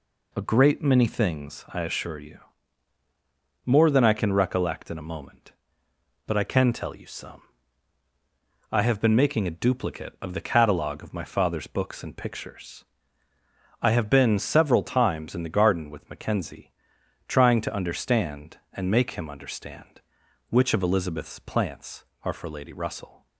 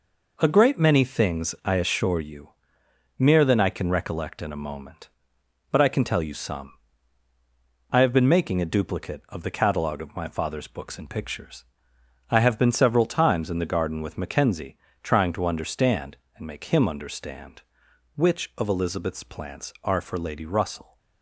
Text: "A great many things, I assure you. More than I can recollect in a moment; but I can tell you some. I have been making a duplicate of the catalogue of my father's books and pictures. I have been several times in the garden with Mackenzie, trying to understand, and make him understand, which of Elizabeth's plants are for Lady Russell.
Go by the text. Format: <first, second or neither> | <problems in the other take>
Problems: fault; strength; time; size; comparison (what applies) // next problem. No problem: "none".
first | says "Mere" for "More"; at 3.1 s